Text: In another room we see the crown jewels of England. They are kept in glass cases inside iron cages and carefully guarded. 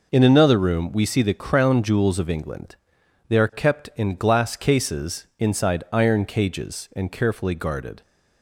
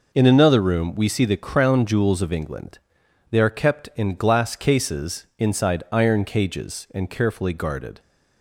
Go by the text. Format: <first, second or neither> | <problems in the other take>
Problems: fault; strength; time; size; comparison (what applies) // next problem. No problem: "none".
neither | none